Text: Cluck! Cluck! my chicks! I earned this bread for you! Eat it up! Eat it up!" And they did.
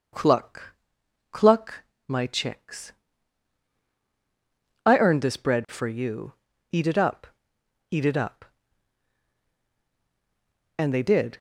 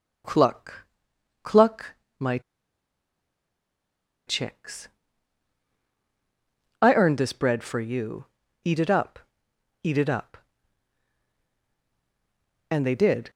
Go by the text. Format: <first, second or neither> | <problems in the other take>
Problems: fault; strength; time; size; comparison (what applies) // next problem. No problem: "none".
first | pauses between "my" and "chicks"; strong; at 2.3 s; 1.8 s long